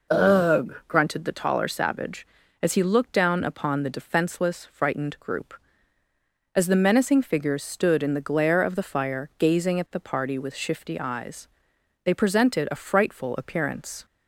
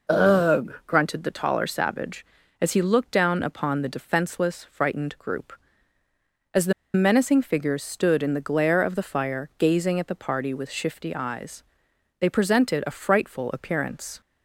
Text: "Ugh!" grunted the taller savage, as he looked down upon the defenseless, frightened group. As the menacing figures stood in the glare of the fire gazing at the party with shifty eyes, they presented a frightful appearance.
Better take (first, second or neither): first